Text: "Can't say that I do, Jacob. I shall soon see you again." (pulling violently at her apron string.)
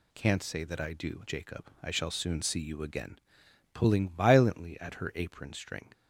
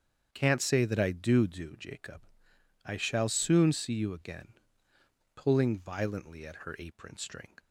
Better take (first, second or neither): first